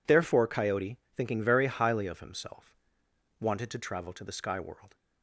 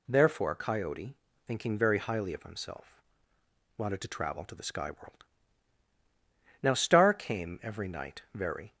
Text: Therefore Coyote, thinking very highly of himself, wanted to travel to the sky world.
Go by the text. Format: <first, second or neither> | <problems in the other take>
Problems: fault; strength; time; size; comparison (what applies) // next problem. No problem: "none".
first | goes on to say "Now Star came every night very"; strong; from 6.6 s on; 2.1 s long